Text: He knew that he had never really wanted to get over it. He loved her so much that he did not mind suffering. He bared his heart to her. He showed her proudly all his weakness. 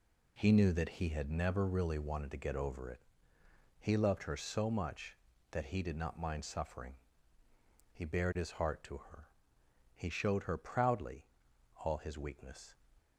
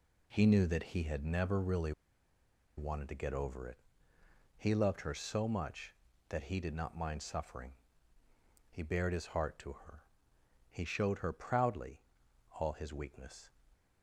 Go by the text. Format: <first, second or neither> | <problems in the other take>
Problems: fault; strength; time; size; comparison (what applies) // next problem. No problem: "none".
first | pauses between "really" and "wanted"; noticeable; at 1.9 s; 0.86 s long // pauses between "proudly" and "all"; noticeable; at 12.0 s; 0.58 s long; noticeable in the first